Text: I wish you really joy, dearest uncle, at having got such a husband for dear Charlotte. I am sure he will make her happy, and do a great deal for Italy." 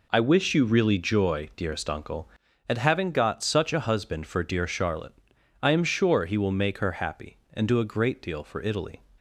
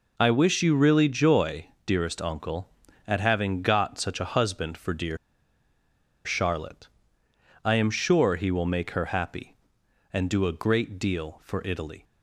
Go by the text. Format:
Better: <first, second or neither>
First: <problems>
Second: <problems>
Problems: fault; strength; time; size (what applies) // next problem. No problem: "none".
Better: first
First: none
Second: pauses between "dear" and "Charlotte"; at 5.1 s; 1.0 s long